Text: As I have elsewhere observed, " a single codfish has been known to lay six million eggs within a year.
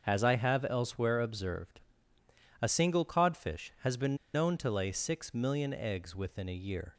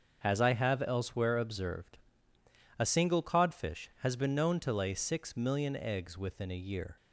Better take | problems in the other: second | starts louder than the rest; until 1.0 s; 7 dB; also in the second // pauses between "been" and "known"; slight; at 4.1 s; 0.19 s long

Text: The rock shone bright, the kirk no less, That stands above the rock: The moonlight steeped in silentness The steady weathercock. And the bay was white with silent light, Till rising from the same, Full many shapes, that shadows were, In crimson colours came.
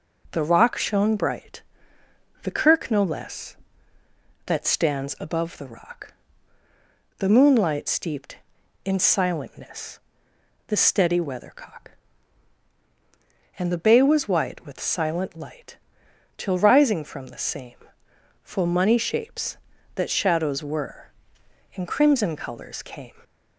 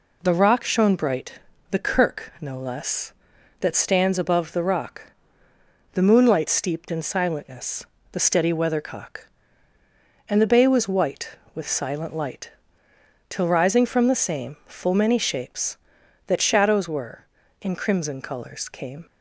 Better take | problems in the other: second | pauses between "silentness" and "The"; noticeable; at 10.0 s; 0.66 s long; slight in the second // says "money" for "many"; at 18.6 s

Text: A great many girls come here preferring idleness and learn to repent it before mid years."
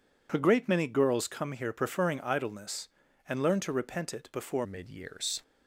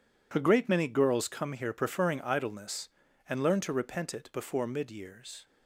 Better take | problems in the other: second | changes voice at "mid"; from 4.6 s on; 0.8 s long

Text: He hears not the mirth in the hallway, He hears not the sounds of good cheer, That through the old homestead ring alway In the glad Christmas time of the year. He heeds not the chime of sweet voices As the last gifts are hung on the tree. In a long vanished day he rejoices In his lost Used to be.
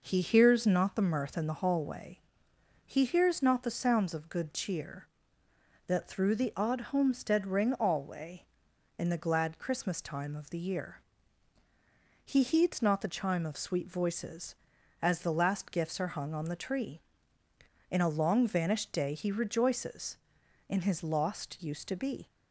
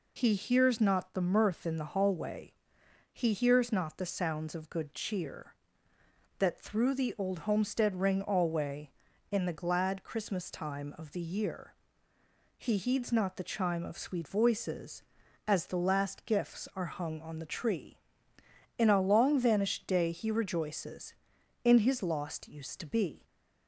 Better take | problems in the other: second | says "odd" for "old"; at 6.5 s

